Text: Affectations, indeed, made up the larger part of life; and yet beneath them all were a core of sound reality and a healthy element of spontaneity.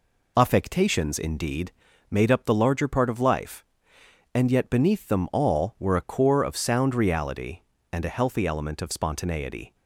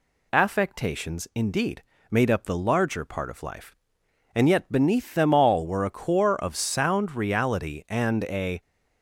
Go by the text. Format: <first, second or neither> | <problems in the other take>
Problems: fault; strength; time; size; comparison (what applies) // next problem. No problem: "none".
first | stops before "healthy element of spontaneity"; at 8.6 s